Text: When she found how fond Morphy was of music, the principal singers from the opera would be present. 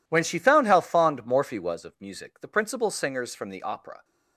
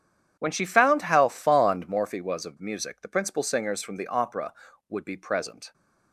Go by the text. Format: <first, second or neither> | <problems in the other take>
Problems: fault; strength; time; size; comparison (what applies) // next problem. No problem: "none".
second | stops before "would be present"; at 4.0 s